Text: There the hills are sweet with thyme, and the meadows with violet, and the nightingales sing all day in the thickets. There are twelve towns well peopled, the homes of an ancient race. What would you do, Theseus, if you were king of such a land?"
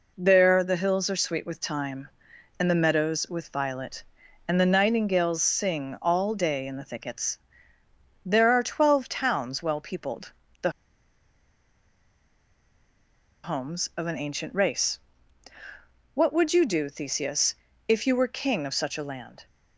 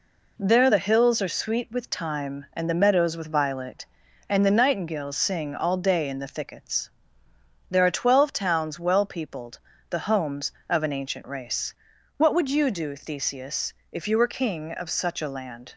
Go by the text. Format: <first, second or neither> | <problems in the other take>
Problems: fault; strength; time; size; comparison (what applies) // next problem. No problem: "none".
second | pauses between "the" and "homes"; strong; at 10.6 s; 2.7 s long